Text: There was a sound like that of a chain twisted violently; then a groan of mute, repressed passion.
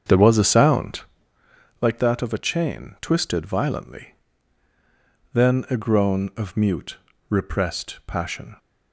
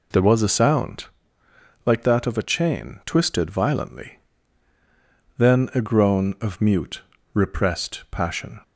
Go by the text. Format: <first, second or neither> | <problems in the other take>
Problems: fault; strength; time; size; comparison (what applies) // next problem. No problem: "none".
second | starts louder than the rest; strong; until 1.4 s; 7.5 dB // pauses between "sound" and "like"; noticeable; at 1.0 s; 0.80 s long; noticeable in the second